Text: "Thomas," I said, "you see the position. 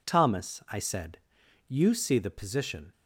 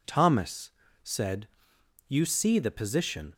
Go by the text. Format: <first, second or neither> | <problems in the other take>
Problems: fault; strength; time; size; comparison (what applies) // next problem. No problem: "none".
first | skips "I"; at 0.8 s